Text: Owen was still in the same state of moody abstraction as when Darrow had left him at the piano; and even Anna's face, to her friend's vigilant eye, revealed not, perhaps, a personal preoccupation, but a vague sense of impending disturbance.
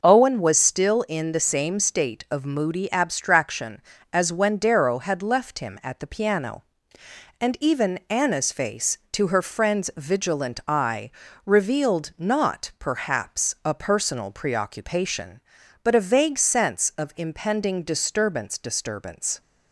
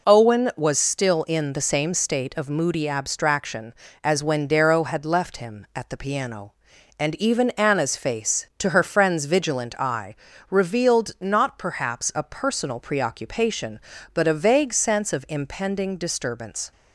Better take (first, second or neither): second